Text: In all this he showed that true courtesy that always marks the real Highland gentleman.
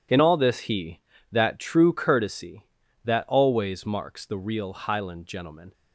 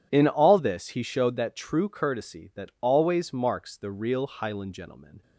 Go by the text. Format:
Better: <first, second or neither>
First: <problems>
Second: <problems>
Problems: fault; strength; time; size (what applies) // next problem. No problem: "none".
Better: second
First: skips "showed"; at 1.1 s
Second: none